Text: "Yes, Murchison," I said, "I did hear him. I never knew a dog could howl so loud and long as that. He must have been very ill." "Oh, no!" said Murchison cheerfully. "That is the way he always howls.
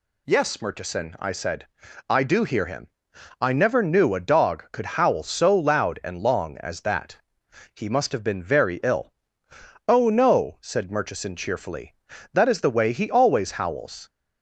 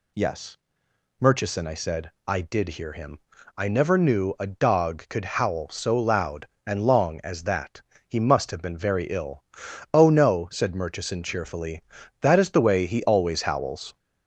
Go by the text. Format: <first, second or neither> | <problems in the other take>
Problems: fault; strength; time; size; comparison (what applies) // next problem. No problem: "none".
second | says "do" for "did"; at 2.2 s